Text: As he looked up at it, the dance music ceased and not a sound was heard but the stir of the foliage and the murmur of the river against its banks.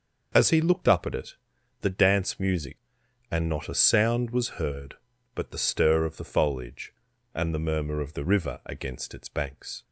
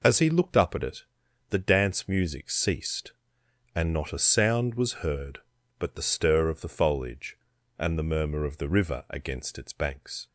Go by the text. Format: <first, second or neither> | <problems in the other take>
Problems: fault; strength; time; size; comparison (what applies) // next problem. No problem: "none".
second | skips "ceased"; at 3.0 s